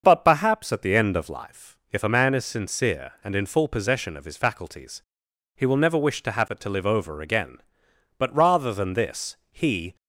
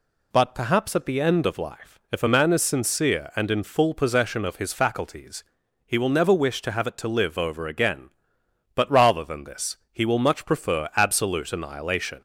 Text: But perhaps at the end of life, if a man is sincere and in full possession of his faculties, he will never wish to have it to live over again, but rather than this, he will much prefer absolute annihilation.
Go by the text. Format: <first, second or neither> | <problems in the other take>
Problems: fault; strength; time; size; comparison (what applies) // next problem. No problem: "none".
second | starts louder than the rest; until 1.0 s; 6.5 dB // stops before "will much prefer absolute annihilation"; at 9.9 s